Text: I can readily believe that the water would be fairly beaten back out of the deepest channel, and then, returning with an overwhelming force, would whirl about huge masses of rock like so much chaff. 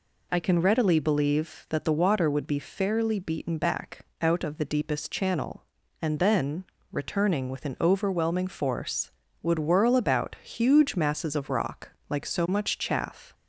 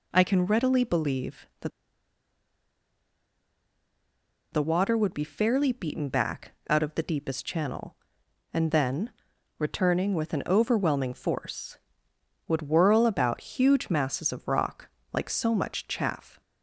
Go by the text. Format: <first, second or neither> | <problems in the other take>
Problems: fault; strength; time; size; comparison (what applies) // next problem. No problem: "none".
first | pauses between "that" and "the"; strong; at 1.7 s; 2.8 s long // pauses between "back" and "out"; slight; at 6.5 s; 0.16 s long; slight in the first // pauses between "rock" and "like"; slight; at 14.8 s; 0.24 s long; slight in the first